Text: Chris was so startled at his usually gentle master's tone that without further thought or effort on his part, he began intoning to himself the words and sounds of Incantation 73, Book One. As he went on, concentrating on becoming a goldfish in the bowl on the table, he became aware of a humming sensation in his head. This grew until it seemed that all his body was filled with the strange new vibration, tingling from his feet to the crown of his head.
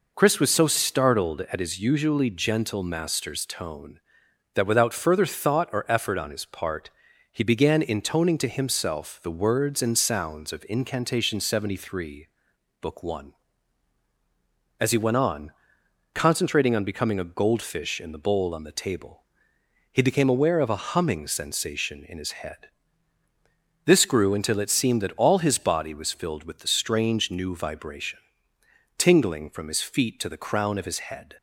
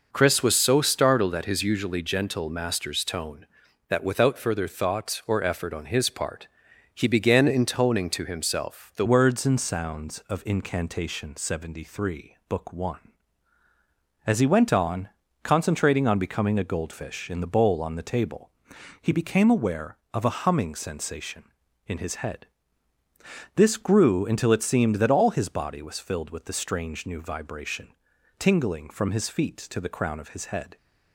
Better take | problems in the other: first | changes voice at "words"; from 9.0 s on; 21.7 s long

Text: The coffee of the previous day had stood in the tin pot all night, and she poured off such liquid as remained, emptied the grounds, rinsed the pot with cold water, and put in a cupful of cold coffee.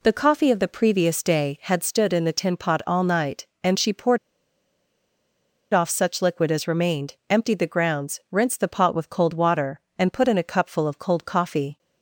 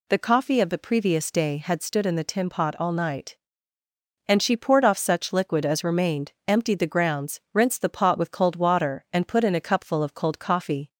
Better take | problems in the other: second | pauses between "poured" and "off"; strong; at 4.1 s; 1.5 s long

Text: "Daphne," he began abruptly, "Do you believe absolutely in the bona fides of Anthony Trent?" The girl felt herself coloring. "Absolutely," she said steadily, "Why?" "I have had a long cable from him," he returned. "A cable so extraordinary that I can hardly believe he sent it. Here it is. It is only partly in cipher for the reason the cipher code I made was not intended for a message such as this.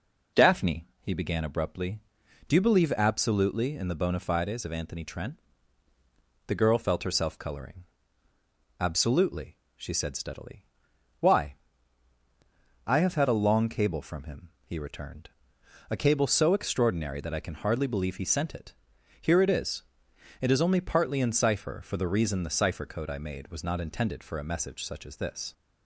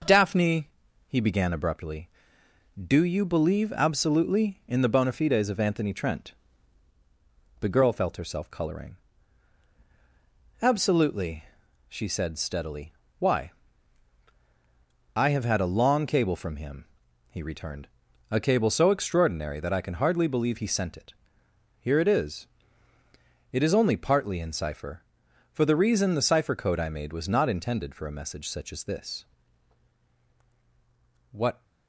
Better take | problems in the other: first | goes on to say "What"; slight; from 31.3 s on; 0.32 s long

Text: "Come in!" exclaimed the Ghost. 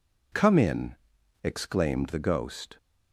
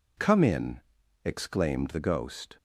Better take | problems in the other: neither | none

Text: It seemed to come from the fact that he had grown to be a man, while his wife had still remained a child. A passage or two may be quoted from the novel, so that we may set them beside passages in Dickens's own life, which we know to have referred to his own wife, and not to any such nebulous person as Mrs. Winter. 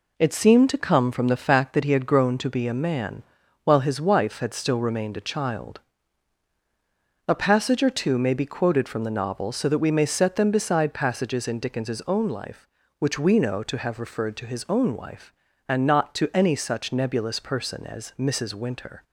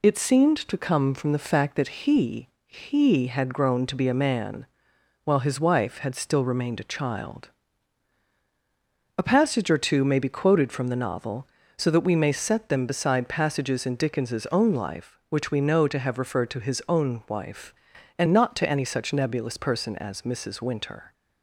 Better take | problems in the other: first | says "he" twice; at 2.6 s

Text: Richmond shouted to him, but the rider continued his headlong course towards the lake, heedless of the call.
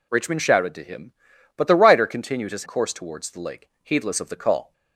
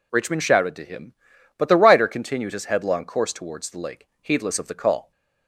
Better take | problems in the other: second | skips "headlong"; at 2.6 s

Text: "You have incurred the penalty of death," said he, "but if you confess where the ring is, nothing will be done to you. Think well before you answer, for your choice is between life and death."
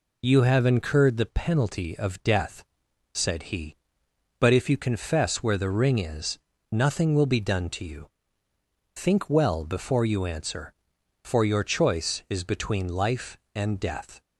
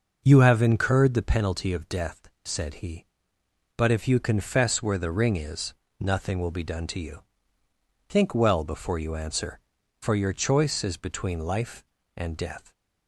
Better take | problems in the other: neither | none

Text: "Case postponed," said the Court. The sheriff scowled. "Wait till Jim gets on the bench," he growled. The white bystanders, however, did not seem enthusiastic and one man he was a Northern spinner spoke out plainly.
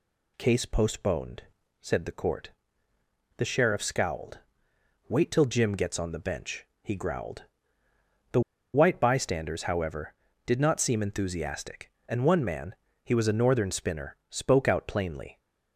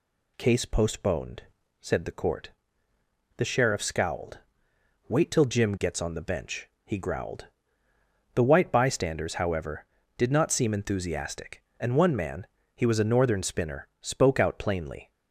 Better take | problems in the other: second | pauses between "The" and "white"; slight; at 8.3 s; 0.33 s long // pauses between "man" and "he"; slight; at 12.7 s; 0.28 s long; slight in the second

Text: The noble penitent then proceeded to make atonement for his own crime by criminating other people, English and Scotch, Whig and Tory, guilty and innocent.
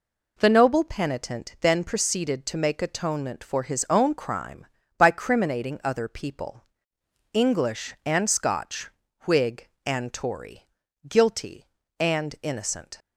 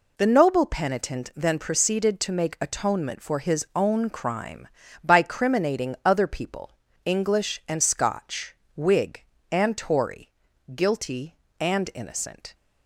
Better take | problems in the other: neither | none

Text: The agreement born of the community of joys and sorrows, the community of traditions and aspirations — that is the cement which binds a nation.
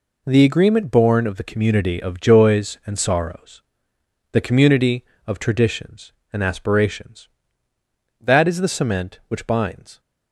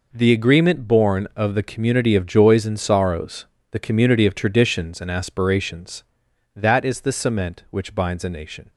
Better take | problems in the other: second | stops before "a nation"; at 9.9 s

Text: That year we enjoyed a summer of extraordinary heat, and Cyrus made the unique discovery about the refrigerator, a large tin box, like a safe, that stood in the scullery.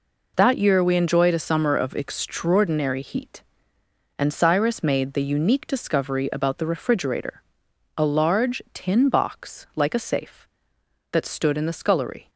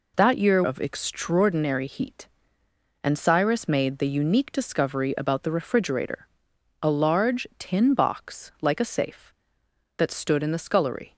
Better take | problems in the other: first | skips "we enjoyed a summer"; at 0.6 s

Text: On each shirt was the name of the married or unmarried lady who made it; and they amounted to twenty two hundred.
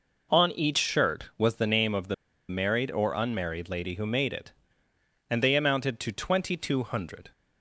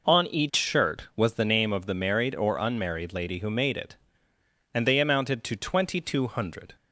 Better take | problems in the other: second | pauses between "the" and "married"; slight; at 2.1 s; 0.35 s long

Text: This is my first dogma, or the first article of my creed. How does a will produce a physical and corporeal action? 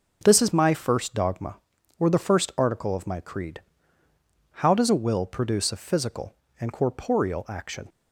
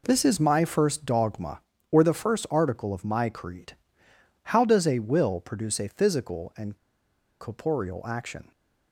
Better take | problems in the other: first | pauses between "and" and "corporeal"; noticeable; at 6.7 s; 0.63 s long

